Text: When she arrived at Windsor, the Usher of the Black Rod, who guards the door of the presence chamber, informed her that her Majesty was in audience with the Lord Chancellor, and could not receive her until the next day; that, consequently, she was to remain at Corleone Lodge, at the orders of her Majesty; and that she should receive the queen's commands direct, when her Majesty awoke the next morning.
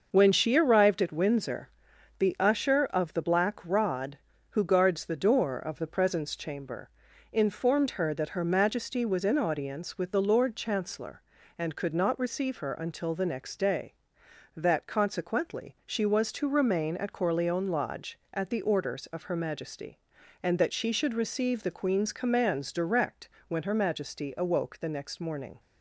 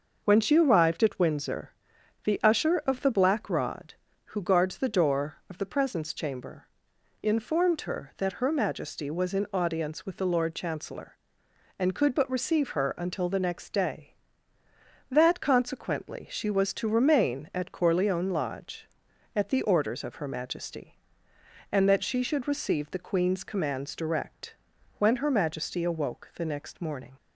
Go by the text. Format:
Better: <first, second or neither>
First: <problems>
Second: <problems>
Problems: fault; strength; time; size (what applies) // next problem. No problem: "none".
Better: first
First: none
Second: starts louder than the rest; noticeable; until 1.2 s; 6 dB // says "but" for "not"; at 12.1 s